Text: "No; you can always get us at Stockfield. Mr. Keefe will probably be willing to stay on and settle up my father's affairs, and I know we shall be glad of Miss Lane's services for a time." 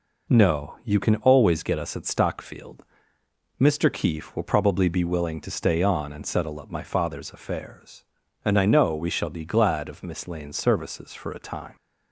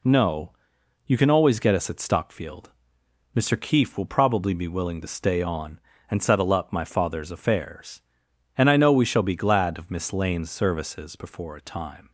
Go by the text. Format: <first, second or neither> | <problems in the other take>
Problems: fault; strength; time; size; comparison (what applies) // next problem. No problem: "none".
first | says "before" for "for"; at 11.1 s